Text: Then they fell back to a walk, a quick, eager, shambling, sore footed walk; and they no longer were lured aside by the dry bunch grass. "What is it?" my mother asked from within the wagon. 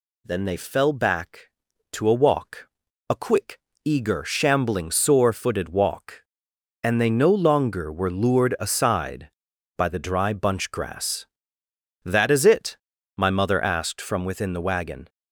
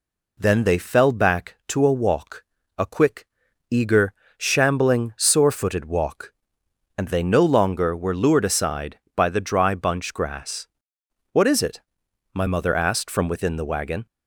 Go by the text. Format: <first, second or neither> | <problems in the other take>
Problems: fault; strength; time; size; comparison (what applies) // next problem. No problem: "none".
second | says "That" for "What"; at 12.0 s